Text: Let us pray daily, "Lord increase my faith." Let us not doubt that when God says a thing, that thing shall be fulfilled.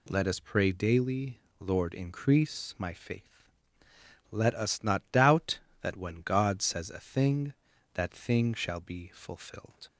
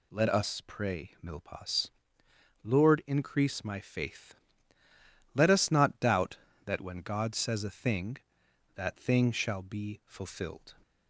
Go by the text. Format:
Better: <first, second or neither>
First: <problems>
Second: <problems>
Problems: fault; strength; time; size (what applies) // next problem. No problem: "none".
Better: first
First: none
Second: says "milpas" for "daily"; at 1.2 s